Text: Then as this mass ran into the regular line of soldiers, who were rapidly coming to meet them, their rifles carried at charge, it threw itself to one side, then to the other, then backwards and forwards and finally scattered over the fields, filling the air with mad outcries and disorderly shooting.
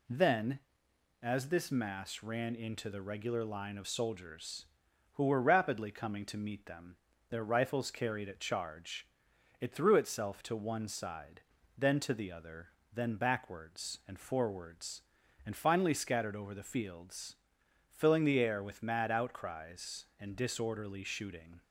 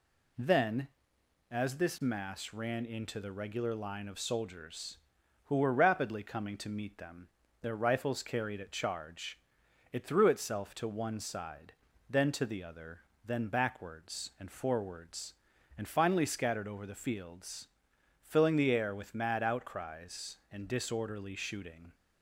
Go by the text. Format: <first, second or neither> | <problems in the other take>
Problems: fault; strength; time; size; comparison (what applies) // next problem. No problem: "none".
neither | none